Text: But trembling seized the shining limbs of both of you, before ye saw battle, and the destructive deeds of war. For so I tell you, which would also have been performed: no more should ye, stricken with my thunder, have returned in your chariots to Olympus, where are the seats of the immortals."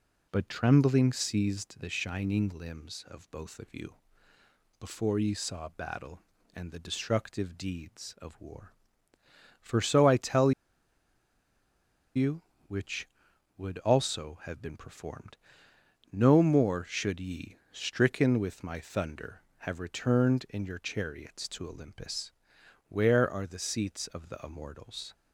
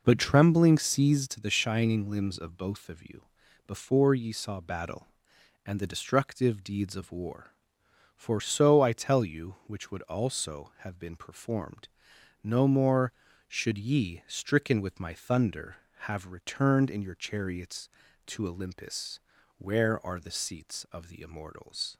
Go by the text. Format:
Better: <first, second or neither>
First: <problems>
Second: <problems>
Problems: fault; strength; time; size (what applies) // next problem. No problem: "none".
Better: second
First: pauses between "tell" and "you"; strong; at 10.5 s; 1.6 s long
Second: none